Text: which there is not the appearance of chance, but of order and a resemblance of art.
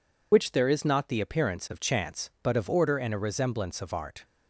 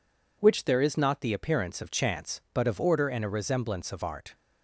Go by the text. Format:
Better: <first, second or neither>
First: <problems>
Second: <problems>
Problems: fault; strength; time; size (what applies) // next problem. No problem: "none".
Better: second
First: loses the start of "which"; at 0.3 s; 55 ms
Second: none